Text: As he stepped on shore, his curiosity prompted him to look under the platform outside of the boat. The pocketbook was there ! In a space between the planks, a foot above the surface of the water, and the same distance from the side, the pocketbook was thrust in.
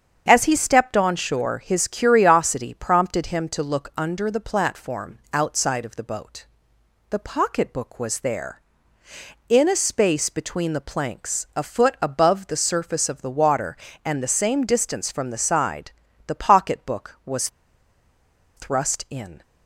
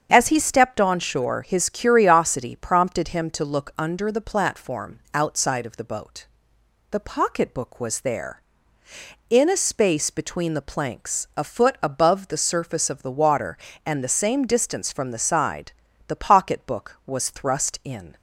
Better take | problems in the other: second | starts louder than the rest; strong; until 1.2 s; 8 dB; strong in the second // pauses between "was" and "thrust"; at 17.4 s; 1.0 s long

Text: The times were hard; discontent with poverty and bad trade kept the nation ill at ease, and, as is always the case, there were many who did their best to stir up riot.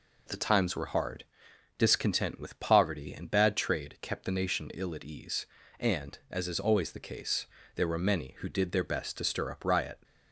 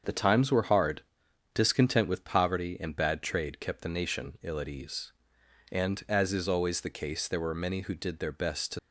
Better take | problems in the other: first | starts louder than the rest; until 1.5 s; 7 dB // stops before "stir up riot"; at 8.7 s

